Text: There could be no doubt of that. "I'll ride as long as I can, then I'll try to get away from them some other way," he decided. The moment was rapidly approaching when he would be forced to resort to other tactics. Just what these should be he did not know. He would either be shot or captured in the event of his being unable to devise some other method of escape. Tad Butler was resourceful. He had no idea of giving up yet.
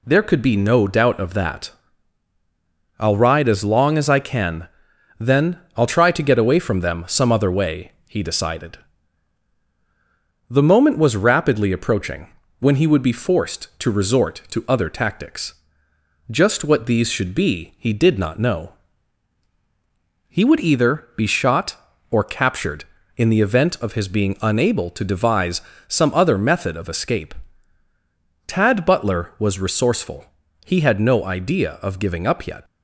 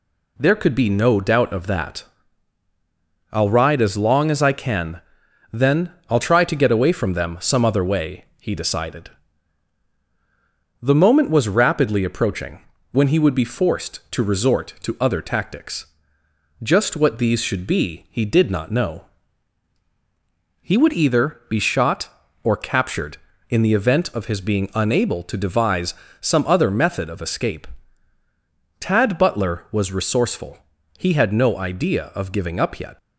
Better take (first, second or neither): neither